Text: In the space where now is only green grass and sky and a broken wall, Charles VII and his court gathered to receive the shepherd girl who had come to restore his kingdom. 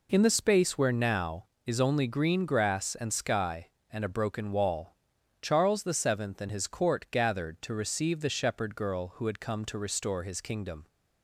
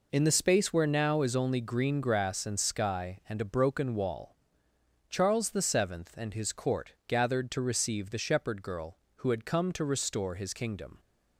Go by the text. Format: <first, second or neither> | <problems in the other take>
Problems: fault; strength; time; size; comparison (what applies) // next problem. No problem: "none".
neither | none